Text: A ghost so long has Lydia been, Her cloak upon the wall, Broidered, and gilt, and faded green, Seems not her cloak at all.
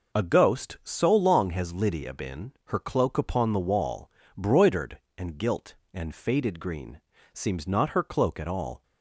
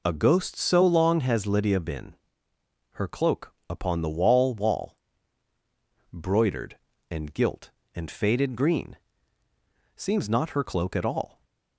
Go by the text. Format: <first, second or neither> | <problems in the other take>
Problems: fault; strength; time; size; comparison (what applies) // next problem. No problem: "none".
first | pauses between "cloak" and "upon"; slight; at 3.5 s; 0.16 s long // says "wall" twice; at 4.5 s